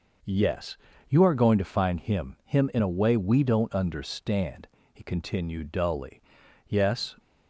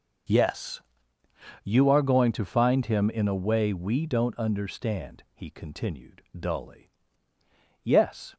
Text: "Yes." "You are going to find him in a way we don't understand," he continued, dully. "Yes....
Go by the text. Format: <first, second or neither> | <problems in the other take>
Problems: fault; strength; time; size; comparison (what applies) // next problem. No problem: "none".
second | says "him" twice; at 2.4 s